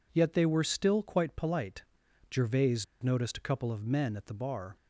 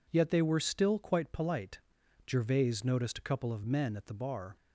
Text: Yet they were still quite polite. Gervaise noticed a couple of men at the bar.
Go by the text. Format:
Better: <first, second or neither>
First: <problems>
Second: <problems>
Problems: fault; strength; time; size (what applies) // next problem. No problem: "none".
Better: second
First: pauses between "Gervaise" and "noticed"; slight; at 2.8 s; 0.18 s long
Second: none